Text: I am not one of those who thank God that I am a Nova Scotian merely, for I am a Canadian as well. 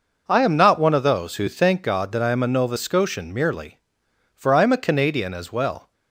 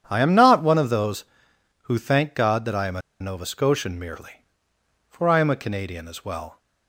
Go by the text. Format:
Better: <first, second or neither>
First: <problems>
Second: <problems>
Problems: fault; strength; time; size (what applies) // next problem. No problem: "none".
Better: first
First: none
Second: starts louder than the rest; strong; until 1.0 s; 9 dB // pauses between "a" and "Nova"; slight; at 3.0 s; 0.19 s long